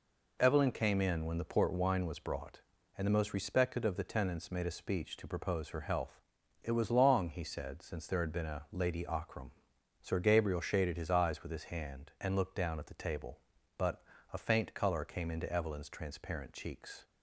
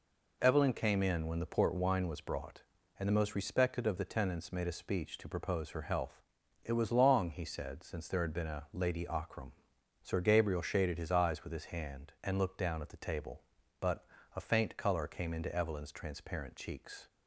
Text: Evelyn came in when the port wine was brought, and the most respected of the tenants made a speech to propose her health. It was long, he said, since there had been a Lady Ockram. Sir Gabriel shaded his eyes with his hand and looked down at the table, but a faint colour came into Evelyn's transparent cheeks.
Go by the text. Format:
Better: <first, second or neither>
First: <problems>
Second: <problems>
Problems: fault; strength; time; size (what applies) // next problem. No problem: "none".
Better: neither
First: pauses between "but" and "a"; slight; at 14.0 s; 0.32 s long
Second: pauses between "but" and "a"; slight; at 14.0 s; 0.32 s long